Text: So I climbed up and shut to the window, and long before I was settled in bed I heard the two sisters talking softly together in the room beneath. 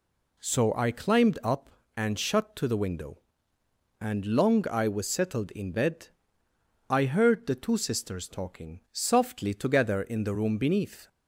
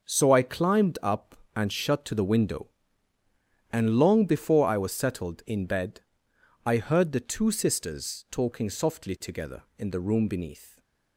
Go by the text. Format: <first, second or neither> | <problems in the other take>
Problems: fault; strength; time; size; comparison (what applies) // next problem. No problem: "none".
second | skips "before"; at 4.6 s // pauses between "bed" and "I"; noticeable; at 6.0 s; 0.82 s long; noticeable in the second